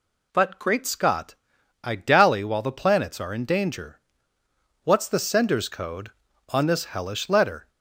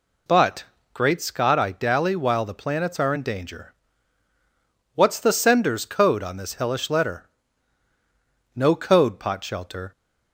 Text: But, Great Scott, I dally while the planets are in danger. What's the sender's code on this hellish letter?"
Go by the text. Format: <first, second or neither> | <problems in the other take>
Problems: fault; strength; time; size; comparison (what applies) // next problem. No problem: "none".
first | goes on to say "No code Potshelter"; from 8.5 s on; 1.3 s long